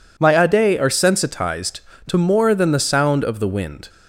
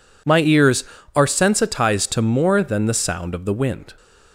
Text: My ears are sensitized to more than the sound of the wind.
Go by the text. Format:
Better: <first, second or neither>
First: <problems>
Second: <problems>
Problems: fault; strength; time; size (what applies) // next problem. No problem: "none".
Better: second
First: says "ade" for "ears"; at 0.4 s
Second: none